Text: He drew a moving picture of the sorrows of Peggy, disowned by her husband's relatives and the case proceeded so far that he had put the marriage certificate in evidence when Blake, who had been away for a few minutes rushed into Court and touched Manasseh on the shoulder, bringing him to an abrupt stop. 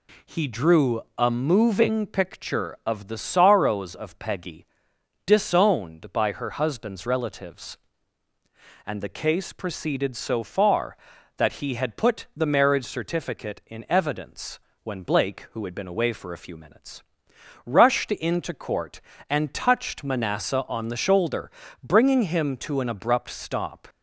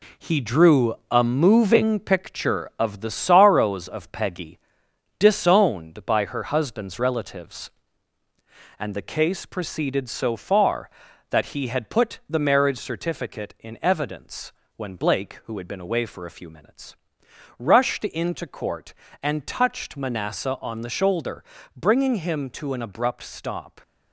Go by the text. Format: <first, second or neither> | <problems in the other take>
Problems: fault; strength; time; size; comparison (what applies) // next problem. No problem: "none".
first | gets quieter; throughout; 6.5 dB // pauses between "drew" and "a"; slight; at 0.9 s; 0.16 s long; slight in the first // pauses between "evidence" and "when"; slight; at 14.5 s; 0.26 s long; slight in the first // pauses between "minutes" and "rushed"; noticeable; at 16.9 s; 0.60 s long; noticeable in the first